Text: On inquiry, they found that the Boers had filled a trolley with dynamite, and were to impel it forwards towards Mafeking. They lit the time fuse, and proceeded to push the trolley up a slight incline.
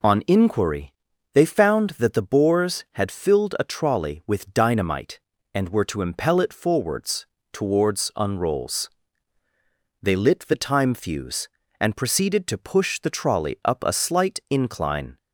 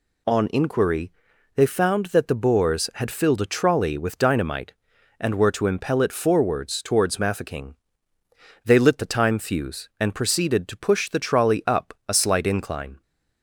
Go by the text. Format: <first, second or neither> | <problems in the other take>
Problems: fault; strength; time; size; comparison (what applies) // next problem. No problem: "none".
second | pauses between "forwards" and "towards"; slight; at 7.2 s; 0.26 s long // says "Unrolls" for "Mafeking"; at 8.1 s